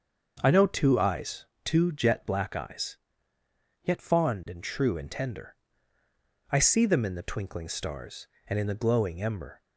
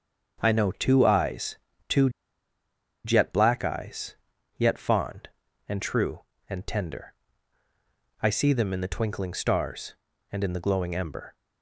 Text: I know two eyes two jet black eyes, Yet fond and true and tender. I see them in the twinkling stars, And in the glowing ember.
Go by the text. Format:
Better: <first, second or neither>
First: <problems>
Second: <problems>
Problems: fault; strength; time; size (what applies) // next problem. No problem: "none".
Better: first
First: starts louder than the rest; until 1.4 s; 6.5 dB // pauses between "eyes" and "two"; slight; at 1.4 s; 0.18 s long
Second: starts louder than the rest; until 1.4 s; 7 dB // pauses between "eyes" and "two"; slight; at 1.5 s; 0.32 s long // pauses between "two" and "jet"; noticeable; at 2.0 s; 0.95 s long